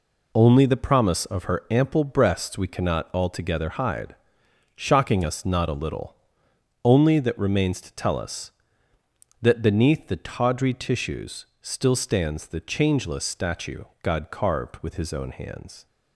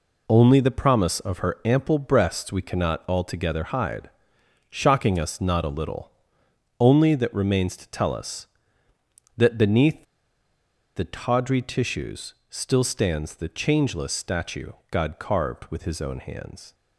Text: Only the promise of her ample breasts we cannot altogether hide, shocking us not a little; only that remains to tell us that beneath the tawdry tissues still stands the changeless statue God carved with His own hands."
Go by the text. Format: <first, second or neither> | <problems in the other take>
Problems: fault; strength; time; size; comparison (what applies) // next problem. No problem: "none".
first | pauses between "beneath" and "the"; noticeable; at 10.0 s; 0.91 s long // pauses between "tissues" and "still"; slight; at 12.3 s; 0.16 s long; slight in the first // pauses between "statue" and "God"; slight; at 14.7 s; 0.18 s long; slight in the first